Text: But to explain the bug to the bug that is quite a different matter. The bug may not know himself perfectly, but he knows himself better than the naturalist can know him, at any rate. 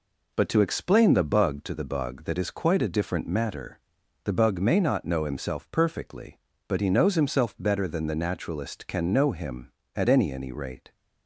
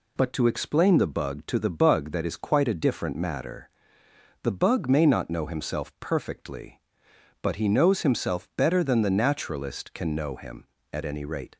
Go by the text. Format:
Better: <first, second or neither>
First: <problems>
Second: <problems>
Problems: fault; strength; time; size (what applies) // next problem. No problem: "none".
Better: second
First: says "any" twice; at 10.3 s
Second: none